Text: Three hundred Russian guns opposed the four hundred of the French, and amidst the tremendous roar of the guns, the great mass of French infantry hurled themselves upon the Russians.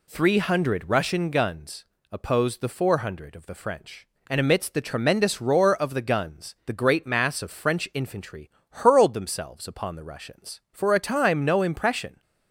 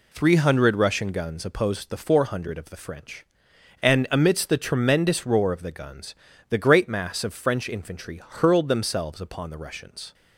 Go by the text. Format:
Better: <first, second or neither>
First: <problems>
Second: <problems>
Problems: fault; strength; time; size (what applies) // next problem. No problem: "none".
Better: second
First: pauses between "guns" and "opposed"; slight; at 1.8 s; 0.26 s long // pauses between "infantry" and "hurled"; slight; at 8.4 s; 0.20 s long // goes on to say "For a time no impression"; from 10.7 s on; 1.5 s long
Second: none